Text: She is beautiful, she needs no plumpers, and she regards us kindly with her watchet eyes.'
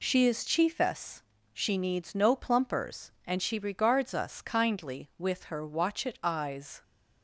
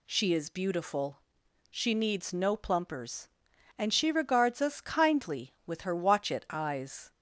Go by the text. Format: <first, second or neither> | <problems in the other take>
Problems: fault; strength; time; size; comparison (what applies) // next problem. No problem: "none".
second | says "chiefess" for "beautiful"; at 0.4 s